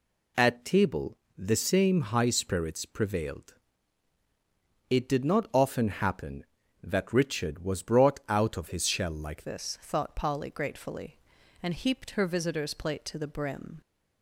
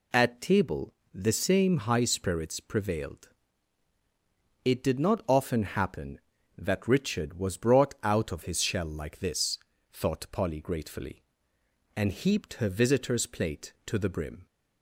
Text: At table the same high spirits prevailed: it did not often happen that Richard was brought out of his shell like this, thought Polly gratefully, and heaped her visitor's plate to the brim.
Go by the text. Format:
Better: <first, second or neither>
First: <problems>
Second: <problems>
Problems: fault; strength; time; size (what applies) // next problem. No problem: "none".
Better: second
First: pauses between "table" and "the"; slight; at 1.1 s; 0.20 s long // changes voice at "this"; from 9.4 s on; 4.4 s long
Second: pauses between "table" and "the"; slight; at 0.9 s; 0.20 s long